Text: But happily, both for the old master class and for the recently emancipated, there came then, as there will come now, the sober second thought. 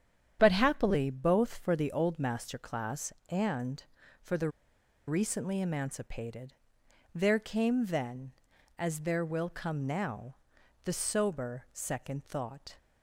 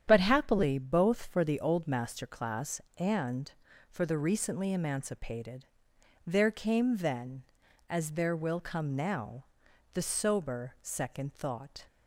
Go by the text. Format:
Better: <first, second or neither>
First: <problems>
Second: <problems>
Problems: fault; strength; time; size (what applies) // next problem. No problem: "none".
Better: second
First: starts louder than the rest; strong; until 1.4 s; 9 dB // pauses between "the" and "recently"; noticeable; at 4.4 s; 0.58 s long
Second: starts louder than the rest; strong; until 1.0 s; 9 dB